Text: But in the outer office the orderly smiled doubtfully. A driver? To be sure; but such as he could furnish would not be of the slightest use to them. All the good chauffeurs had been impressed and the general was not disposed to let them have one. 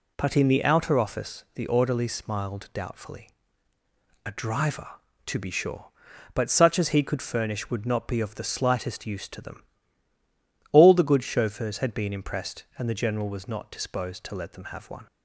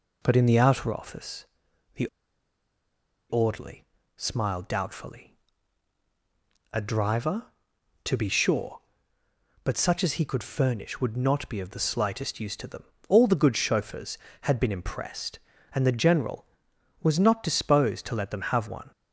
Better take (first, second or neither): first